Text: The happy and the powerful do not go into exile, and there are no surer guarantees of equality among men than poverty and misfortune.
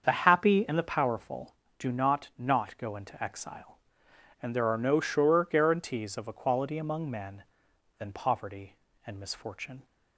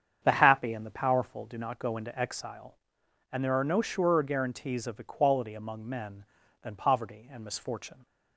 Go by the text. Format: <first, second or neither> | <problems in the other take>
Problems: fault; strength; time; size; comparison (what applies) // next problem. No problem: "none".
second | starts louder than the rest; until 1.0 s; 7 dB; strong in the second // says "not" twice; at 2.3 s